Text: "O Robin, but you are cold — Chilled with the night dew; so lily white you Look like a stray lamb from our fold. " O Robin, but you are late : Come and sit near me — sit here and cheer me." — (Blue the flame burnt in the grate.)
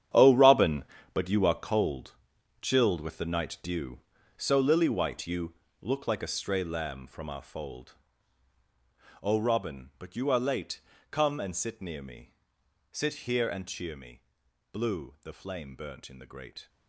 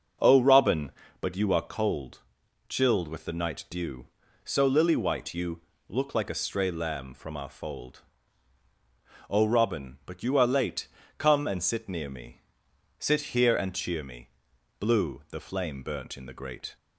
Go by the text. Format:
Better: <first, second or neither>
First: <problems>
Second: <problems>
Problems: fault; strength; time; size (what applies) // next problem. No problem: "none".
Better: second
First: gets quieter; strong; throughout; 14 dB // starts louder than the rest; strong; until 1.4 s; 10.5 dB // pauses between "you" and "Look"; slight; at 5.5 s; 0.26 s long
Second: starts louder than the rest; strong; until 1.5 s; 7.5 dB // pauses between "you" and "Look"; slight; at 5.6 s; 0.26 s long